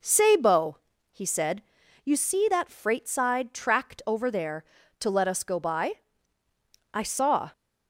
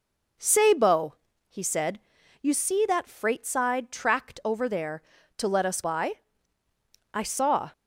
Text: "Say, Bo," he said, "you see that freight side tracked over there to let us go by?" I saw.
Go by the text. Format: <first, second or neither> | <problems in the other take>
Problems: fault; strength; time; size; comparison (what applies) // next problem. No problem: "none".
first | skips "go"; at 5.8 s